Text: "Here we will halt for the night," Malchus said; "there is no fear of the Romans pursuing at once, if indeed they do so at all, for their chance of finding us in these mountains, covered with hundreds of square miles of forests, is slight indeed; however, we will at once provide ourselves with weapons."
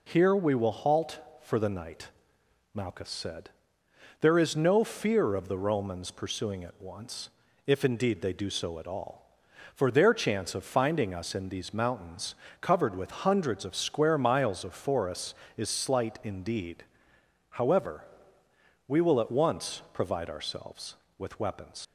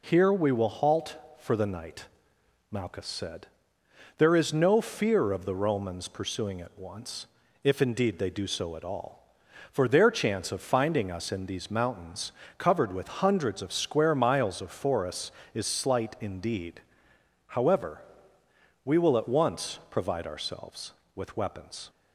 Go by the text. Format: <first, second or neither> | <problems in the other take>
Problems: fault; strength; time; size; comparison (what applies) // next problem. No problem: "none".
second | leaves "weapons" unfinished; at 21.8 s; 75 ms